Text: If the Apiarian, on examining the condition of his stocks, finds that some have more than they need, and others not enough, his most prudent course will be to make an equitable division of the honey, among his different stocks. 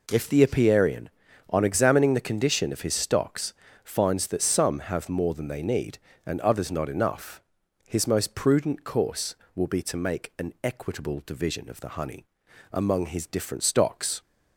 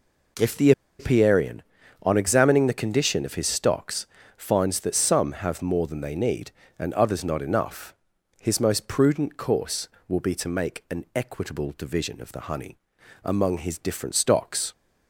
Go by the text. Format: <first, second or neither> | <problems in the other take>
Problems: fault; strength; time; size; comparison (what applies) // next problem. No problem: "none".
first | pauses between "the" and "Apiarian"; slight; at 0.7 s; 0.27 s long